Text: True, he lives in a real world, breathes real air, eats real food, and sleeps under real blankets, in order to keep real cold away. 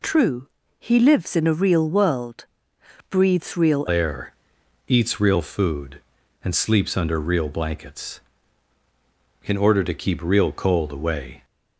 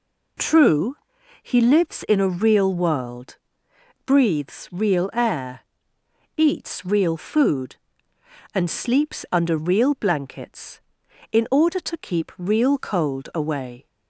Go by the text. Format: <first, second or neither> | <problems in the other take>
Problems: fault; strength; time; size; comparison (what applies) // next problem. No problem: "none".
second | changes voice at "air"; from 3.8 s on; 7.6 s long